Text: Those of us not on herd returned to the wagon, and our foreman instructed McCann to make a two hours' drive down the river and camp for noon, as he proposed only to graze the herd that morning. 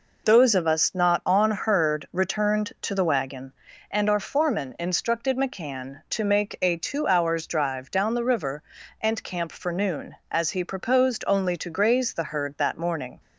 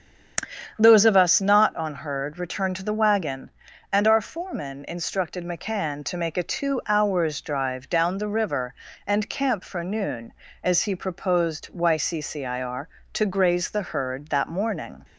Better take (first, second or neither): first